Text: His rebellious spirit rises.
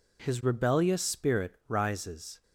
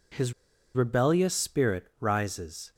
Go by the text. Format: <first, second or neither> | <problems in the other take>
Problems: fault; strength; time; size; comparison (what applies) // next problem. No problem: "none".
first | pauses between "His" and "rebellious"; at 0.3 s; 0.42 s long